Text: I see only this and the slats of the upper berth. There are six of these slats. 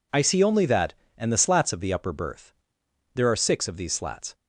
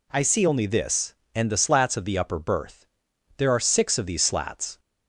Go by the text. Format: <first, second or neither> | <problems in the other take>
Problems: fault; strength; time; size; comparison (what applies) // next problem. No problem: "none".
second | says "that" for "this"; at 0.6 s